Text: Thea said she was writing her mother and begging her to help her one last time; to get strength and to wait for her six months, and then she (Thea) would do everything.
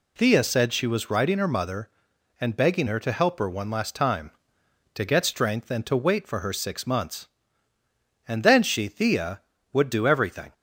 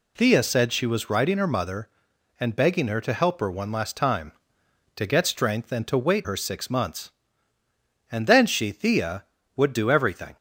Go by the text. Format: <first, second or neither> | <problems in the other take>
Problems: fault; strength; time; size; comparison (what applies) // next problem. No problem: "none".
first | skips "for"; at 6.2 s